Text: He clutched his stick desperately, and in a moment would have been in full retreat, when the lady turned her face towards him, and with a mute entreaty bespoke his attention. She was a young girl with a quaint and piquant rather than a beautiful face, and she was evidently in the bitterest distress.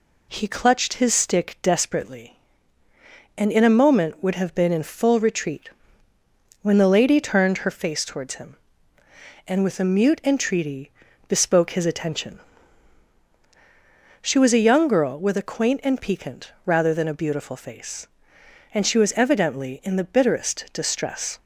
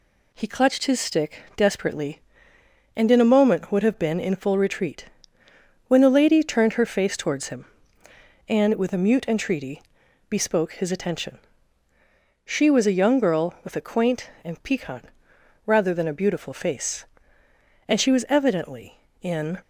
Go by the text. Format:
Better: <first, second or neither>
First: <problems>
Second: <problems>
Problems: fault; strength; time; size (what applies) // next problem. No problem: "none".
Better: first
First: pauses between "entreaty" and "bespoke"; slight; at 10.9 s; 0.36 s long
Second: pauses between "entreaty" and "bespoke"; noticeable; at 9.8 s; 0.48 s long // pauses between "piquant" and "rather"; noticeable; at 15.0 s; 0.60 s long // stops before "the bitterest distress"; at 19.6 s